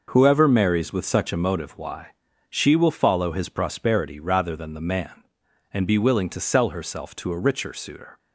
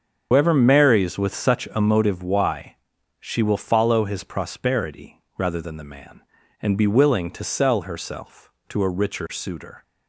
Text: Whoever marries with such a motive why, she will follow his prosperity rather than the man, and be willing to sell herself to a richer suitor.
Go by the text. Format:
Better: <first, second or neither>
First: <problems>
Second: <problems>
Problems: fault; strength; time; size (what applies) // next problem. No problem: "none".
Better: first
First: none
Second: loses the start of "Whoever"; at 0.3 s; 65 ms // starts louder than the rest; until 1.3 s; 7 dB // pauses between "prosperity" and "rather"; slight; at 5.2 s; 0.16 s long